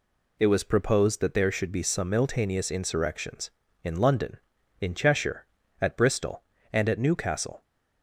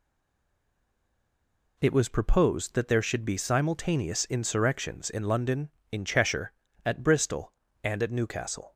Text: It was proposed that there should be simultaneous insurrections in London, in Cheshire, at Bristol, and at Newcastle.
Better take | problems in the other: first | stays silent before the first word; noticeable; until 1.7 s; 1.7 s long

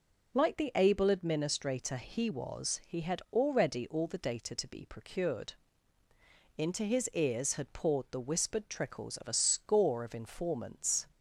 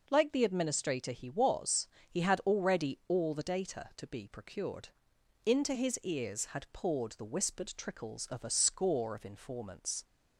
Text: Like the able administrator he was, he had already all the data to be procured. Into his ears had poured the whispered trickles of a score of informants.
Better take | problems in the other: first | skips "able"; at 0.4 s

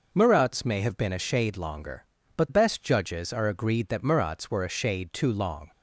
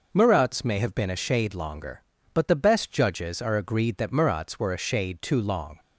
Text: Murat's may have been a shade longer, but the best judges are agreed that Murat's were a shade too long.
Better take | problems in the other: second | skips "the"; at 2.4 s

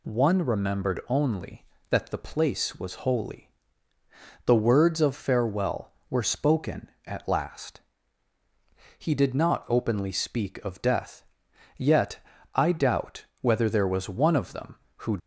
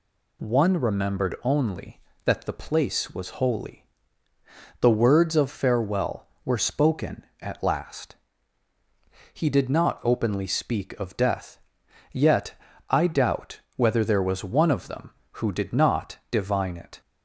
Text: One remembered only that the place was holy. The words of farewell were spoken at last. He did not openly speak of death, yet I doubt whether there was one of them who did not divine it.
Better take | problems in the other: second | pauses between "yet" and "I"; slight; at 12.1 s; 0.34 s long; slight in the second // pauses between "doubt" and "whether"; slight; at 13.2 s; 0.16 s long; slight in the second // stops before "did not divine it"; at 15.1 s

